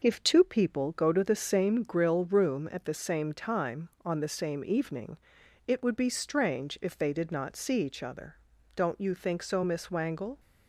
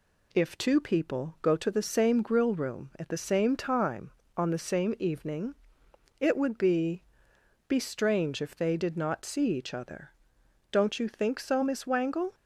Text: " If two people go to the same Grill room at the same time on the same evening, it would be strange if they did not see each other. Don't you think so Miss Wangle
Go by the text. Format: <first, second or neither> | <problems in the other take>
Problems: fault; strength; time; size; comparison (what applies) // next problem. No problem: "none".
first | says "be" twice; at 7.6 s